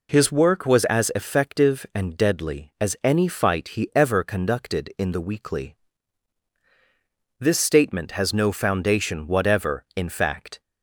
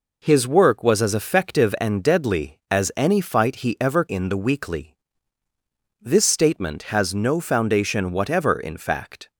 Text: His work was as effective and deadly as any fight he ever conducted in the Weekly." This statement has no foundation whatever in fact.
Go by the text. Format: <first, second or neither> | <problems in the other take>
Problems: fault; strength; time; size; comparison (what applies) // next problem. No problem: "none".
first | skips "conducted"; at 4.0 s